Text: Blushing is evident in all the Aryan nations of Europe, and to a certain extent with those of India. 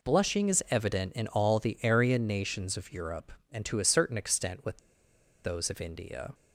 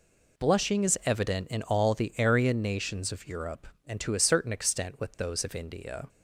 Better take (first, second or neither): second